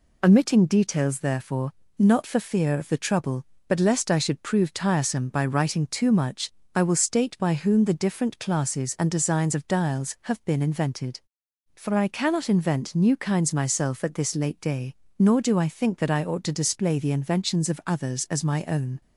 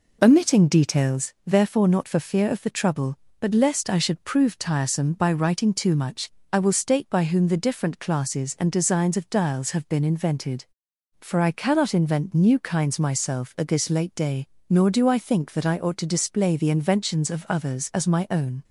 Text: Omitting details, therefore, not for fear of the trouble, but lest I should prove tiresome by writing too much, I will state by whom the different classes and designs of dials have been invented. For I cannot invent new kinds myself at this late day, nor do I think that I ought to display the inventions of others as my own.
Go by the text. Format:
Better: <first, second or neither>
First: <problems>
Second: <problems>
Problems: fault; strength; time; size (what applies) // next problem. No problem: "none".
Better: first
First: none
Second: starts louder than the rest; noticeable; until 1.2 s; 4.5 dB